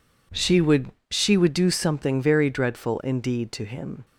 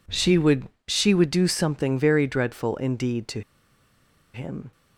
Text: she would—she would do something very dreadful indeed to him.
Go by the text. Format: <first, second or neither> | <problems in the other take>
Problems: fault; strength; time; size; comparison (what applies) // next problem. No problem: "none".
first | pauses between "to" and "him"; noticeable; at 3.4 s; 0.93 s long